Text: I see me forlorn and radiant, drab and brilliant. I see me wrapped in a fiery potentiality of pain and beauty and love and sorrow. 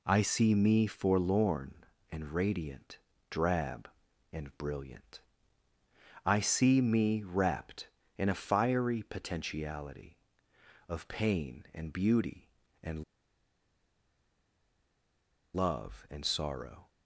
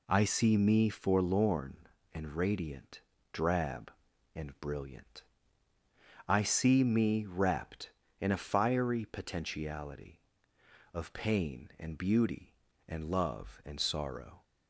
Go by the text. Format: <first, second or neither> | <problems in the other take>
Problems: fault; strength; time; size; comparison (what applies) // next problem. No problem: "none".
second | pauses between "and" and "love"; strong; at 13.0 s; 2.5 s long